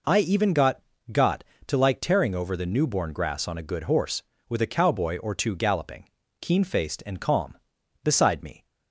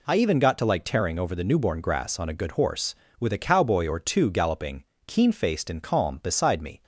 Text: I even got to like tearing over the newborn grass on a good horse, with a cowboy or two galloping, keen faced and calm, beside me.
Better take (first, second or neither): second